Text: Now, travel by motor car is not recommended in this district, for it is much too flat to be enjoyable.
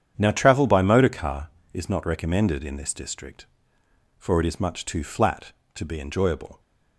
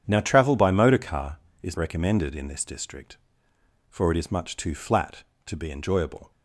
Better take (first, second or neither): first